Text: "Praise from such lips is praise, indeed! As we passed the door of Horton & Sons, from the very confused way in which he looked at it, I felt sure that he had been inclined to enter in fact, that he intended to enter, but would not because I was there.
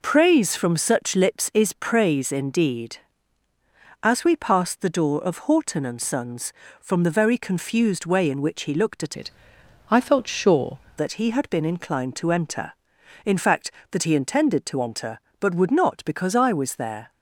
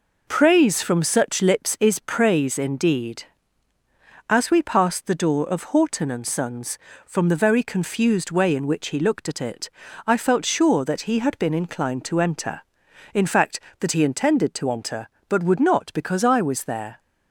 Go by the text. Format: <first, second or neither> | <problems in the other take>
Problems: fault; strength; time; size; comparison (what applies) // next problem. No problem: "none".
second | changes voice from "it" to "sure"; from 9.1 to 10.7 s; 1.6 s long